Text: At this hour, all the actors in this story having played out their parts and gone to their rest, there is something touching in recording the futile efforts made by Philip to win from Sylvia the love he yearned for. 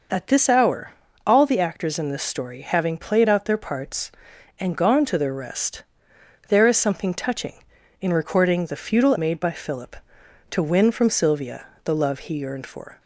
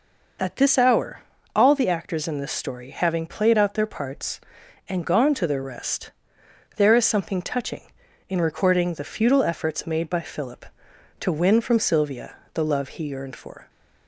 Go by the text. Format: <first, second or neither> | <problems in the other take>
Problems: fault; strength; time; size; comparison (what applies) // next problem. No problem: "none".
second | skips "efforts"; at 9.1 s // pauses between "Sylvia" and "the"; slight; at 11.6 s; 0.16 s long; slight in the second